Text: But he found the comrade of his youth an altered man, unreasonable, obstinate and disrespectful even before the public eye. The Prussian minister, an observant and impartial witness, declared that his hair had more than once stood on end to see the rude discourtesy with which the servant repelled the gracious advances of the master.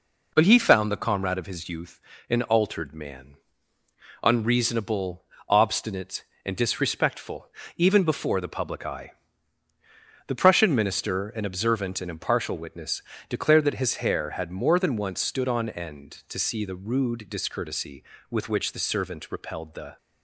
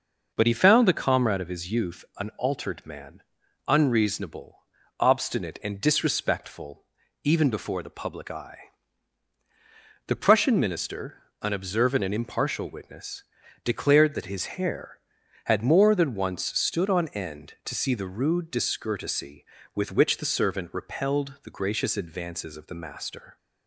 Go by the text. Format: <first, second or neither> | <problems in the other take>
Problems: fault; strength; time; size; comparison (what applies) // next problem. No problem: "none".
second | pauses between "youth" and "an"; slight; at 2.0 s; 0.28 s long // pauses between "disrespectful" and "even"; slight; at 7.4 s; 0.30 s long; also in the second // stops before "gracious advances of the master"; at 19.9 s